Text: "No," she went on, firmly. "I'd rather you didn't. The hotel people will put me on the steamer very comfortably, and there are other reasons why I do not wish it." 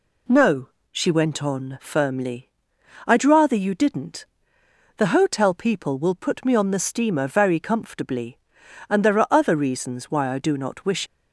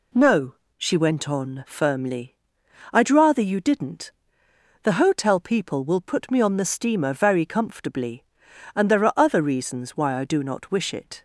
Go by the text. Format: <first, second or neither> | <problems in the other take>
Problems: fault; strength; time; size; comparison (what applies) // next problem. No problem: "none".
second | stops before "it"; at 11.0 s